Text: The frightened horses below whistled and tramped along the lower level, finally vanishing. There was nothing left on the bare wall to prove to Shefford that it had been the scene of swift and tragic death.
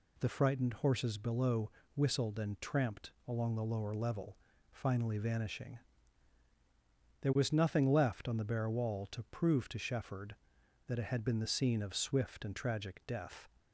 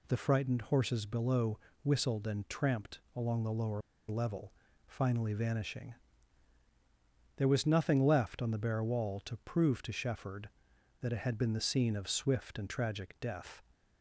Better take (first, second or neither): first